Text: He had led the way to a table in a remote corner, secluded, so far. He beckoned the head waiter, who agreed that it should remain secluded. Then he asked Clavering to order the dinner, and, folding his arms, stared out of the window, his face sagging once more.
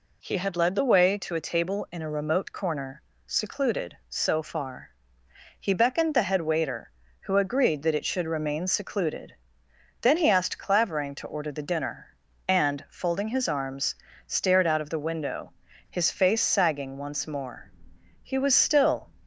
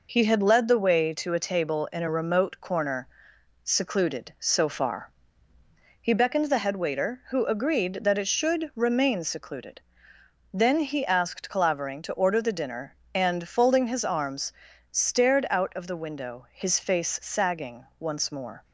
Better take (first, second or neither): second